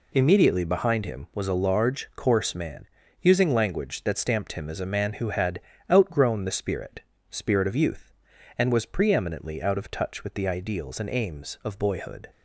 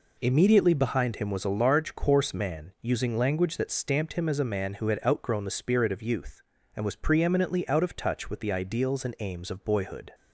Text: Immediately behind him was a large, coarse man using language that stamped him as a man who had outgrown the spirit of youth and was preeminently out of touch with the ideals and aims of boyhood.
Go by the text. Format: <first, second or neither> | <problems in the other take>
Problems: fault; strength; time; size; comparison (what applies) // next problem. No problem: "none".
second | pauses between "man" and "using"; at 2.8 s; 0.38 s long // pauses between "had" and "outgrown"; slight; at 5.5 s; 0.32 s long // says "spirit" twice; at 7.2 s